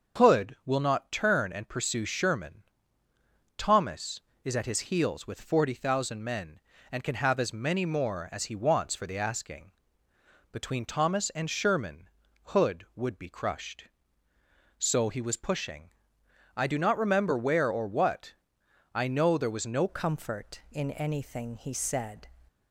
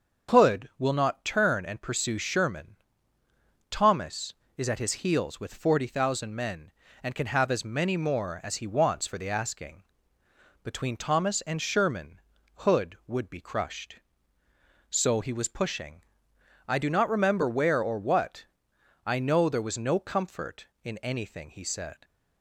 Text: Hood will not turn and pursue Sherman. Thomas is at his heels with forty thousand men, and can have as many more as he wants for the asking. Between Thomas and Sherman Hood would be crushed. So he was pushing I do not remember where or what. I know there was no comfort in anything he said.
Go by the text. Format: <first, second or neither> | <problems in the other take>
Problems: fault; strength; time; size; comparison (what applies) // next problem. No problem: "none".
second | starts louder than the rest; until 1.2 s; 6.5 dB; also in the second // pauses between "Sherman" and "Hood"; slight; at 12.0 s; 0.36 s long; slight in the second // pauses between "pushing" and "I"; noticeable; at 15.9 s; 0.66 s long; noticeable in the second // changes voice at "comfort"; from 19.8 s on; 2.4 s long